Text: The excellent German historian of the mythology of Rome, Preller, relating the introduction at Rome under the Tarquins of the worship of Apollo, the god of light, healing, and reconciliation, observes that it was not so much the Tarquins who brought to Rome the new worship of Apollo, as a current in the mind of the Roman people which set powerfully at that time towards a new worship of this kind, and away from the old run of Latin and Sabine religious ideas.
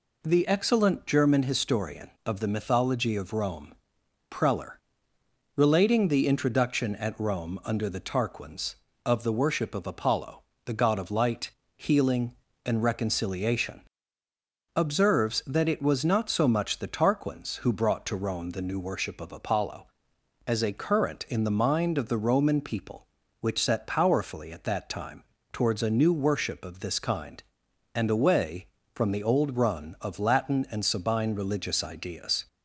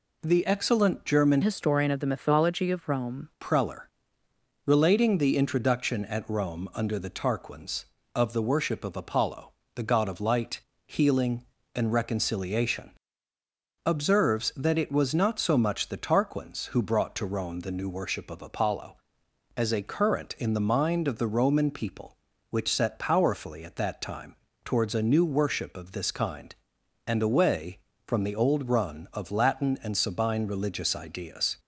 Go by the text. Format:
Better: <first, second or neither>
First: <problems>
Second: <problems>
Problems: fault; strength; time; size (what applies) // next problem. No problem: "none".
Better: first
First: pauses between "time" and "towards"; slight; at 25.2 s; 0.28 s long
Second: changes voice from "historian" to "Rome"; from 1.4 to 3.2 s; 1.8 s long // pauses between "time" and "towards"; slight; at 24.3 s; 0.28 s long